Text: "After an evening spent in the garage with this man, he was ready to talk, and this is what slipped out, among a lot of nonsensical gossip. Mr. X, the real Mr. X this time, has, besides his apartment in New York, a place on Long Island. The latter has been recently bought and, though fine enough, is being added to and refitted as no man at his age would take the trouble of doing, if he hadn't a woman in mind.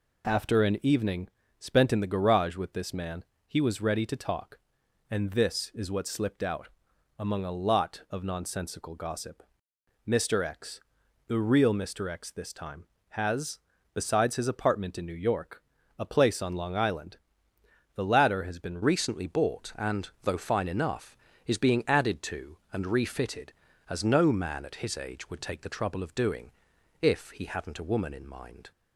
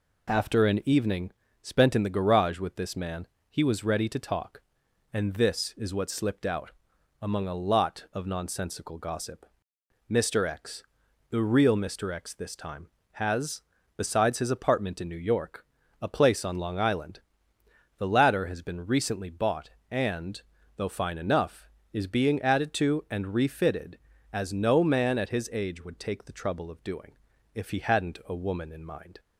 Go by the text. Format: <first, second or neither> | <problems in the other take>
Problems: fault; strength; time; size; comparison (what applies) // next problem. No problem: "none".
second | pauses between "evening" and "spent"; slight; at 1.2 s; 0.32 s long; slight in the second // changes voice at "recently"; from 18.8 s on; 9.9 s long